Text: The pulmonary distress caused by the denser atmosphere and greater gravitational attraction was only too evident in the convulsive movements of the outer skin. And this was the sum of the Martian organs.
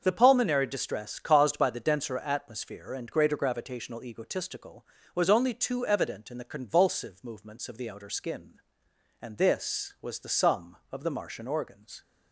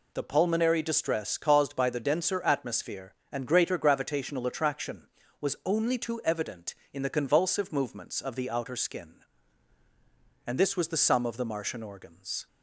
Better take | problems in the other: second | starts louder than the rest; until 1.0 s; 6.5 dB // says "egotistical" for "attraction"; at 4.0 s

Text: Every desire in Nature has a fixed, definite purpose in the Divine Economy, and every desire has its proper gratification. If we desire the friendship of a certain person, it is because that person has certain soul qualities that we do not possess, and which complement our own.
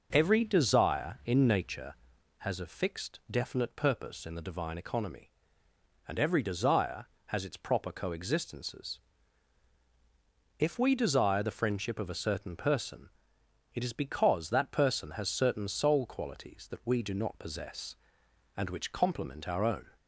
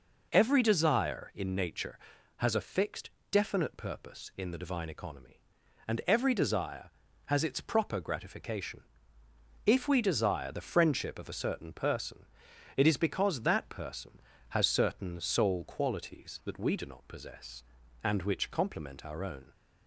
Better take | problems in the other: second | says "coexistences" for "gratification"; at 7.9 s

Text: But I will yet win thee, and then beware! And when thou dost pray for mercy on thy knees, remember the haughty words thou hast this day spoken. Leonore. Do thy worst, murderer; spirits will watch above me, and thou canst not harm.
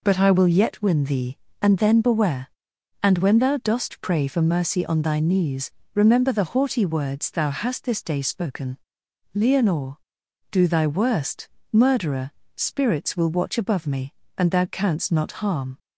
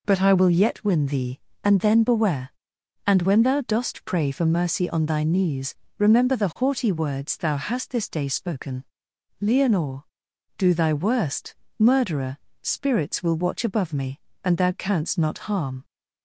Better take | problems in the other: neither | none

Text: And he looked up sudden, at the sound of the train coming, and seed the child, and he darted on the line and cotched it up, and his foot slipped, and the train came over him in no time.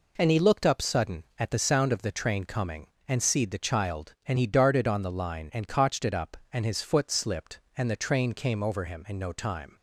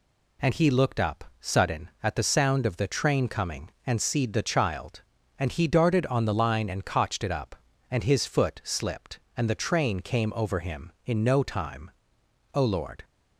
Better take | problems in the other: first | pauses between "up" and "sudden"; slight; at 1.2 s; 0.16 s long // goes on to say "O Lord"; from 12.5 s on; 0.50 s long

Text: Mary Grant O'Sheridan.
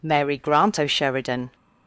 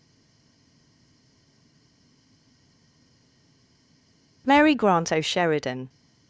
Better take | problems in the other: first | stays silent before the first word; strong; until 4.4 s; 4.4 s long

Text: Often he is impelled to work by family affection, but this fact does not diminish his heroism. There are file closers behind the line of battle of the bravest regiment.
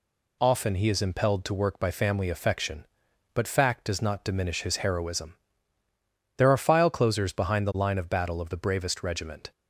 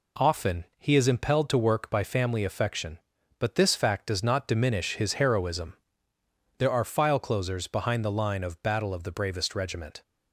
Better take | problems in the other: second | skips "this"; at 3.4 s

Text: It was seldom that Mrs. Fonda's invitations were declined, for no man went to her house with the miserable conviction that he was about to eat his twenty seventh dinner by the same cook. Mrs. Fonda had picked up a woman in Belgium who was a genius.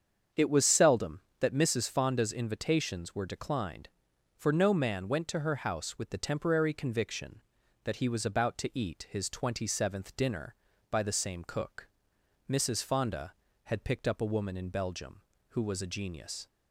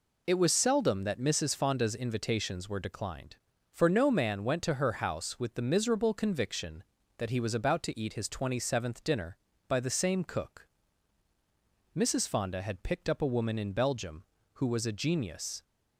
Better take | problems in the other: second | starts louder than the rest; strong; until 1.5 s; 7.5 dB // says "temporary" for "miserable"; at 6.1 s

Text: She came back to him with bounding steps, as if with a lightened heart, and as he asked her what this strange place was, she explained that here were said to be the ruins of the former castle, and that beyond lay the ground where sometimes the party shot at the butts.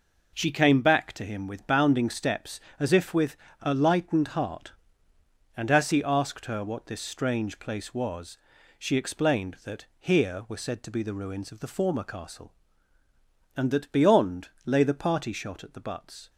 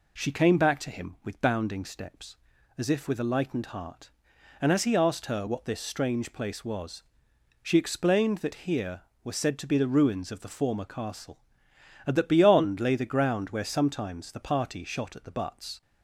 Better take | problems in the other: second | pauses between "with" and "a"; slight; at 3.3 s; 0.26 s long // pauses between "that" and "here"; slight; at 9.8 s; 0.16 s long // pauses between "beyond" and "lay"; slight; at 14.4 s; 0.16 s long // skips "the ground where sometimes"; at 14.8 s

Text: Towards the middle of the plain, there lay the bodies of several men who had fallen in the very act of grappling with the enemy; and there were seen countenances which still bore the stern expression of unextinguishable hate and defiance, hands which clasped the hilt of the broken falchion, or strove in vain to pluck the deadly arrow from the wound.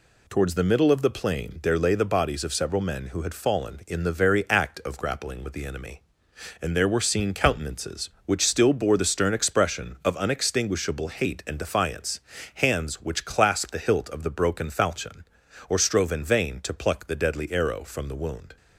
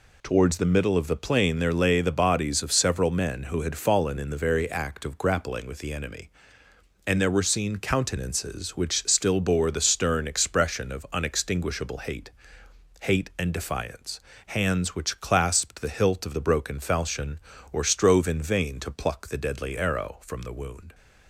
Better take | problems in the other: first | says "hate" twice; at 13.0 s

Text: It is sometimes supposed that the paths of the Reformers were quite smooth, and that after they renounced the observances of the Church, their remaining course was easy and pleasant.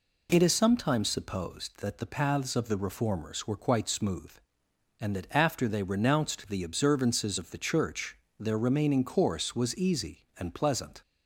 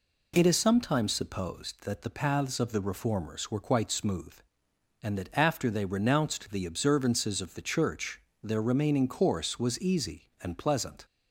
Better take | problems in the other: neither | none

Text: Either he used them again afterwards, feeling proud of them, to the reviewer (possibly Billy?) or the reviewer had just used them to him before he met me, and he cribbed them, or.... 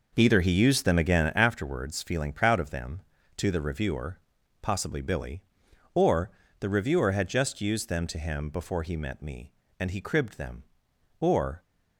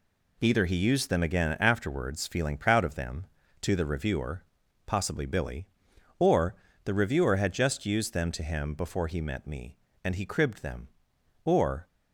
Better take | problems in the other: second | starts louder than the rest; noticeable; until 1.5 s; 5.5 dB // pauses between "or" and "the"; slight; at 6.2 s; 0.30 s long; slight in the second

